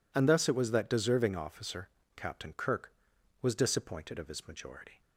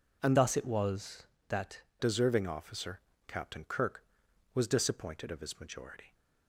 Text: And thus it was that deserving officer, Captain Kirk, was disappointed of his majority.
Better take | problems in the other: first | changes voice from "thus" to "that"; from 0.3 to 1.8 s; 1.5 s long

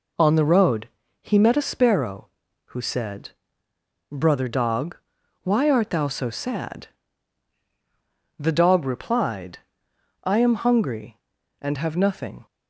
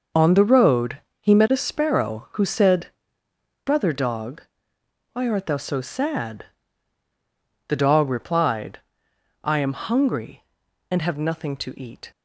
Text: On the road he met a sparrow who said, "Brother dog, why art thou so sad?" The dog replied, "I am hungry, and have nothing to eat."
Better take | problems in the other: second | pauses between "road" and "he"; slight; at 0.8 s; 0.32 s long; slight in the second // stops before "to eat"; at 12.4 s

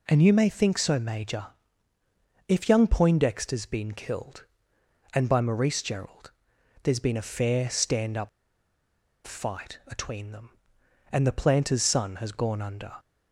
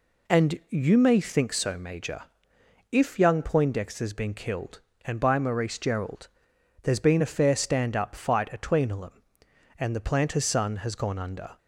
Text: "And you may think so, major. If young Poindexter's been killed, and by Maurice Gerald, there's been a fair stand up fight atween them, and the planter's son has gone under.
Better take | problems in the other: second | pauses between "up" and "fight"; noticeable; at 8.2 s; 0.96 s long

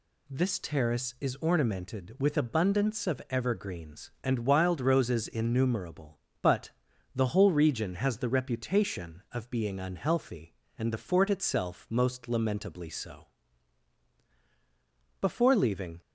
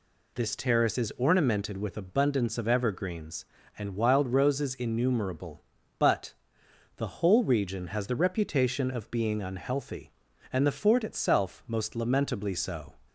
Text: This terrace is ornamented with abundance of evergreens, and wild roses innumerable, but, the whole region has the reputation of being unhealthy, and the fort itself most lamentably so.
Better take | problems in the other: second | goes on to say "Before leaving"; noticeable; from 15.2 s on; 0.80 s long

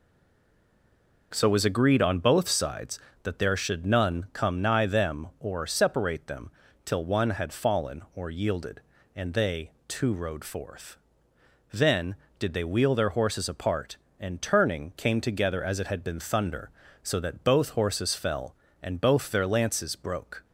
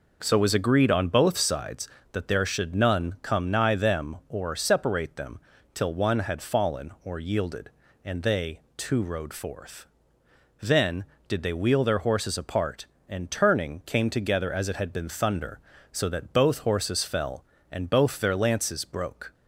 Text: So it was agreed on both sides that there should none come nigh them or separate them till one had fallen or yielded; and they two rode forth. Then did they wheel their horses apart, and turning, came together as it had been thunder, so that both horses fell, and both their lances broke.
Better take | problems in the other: second | stays silent before the first word; noticeable; until 1.3 s; 1.3 s long // pauses between "them" and "till"; slight; at 6.5 s; 0.34 s long; slight in the second // pauses between "they" and "two"; slight; at 9.7 s; 0.18 s long; slight in the second

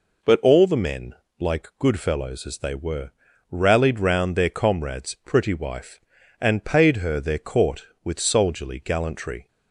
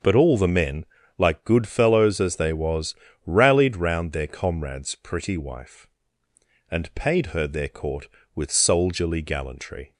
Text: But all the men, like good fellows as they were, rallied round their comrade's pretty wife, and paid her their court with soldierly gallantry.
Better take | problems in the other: first | starts louder than the rest; until 1.3 s; 6.5 dB // says "was" for "were"; at 2.5 s

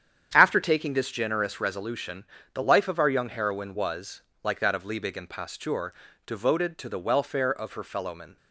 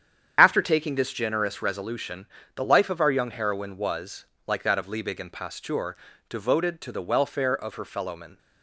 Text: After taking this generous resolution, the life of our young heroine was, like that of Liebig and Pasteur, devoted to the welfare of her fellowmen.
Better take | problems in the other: first | loses the start of "After"; at 0.3 s; 55 ms // starts louder than the rest; strong; until 1.3 s; 8.5 dB; strong in the first

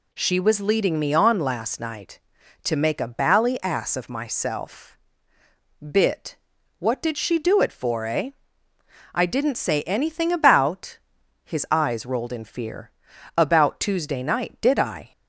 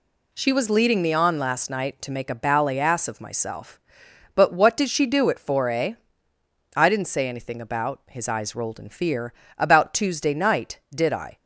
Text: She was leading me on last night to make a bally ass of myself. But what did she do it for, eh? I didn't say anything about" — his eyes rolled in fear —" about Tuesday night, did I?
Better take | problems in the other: second | says "Bit" for "But"; at 5.7 s

